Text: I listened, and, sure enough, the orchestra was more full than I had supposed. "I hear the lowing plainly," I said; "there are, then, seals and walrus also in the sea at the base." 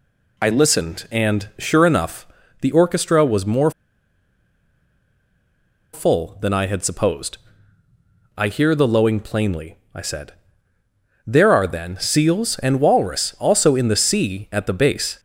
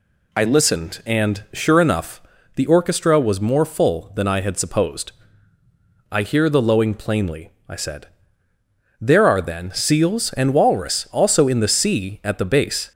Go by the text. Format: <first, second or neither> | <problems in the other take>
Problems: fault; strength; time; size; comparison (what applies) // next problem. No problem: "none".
second | pauses between "more" and "full"; strong; at 3.7 s; 2.2 s long